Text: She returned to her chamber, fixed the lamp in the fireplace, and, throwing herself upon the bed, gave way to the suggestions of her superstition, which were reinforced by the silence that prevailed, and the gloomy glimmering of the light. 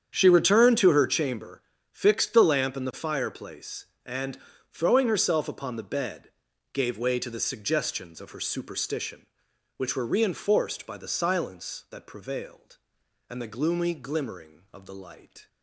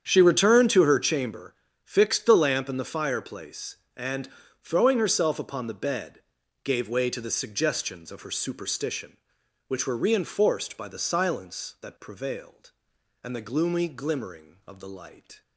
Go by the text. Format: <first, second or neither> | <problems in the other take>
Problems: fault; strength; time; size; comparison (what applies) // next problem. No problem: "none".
neither | starts louder than the rest; strong; the same in both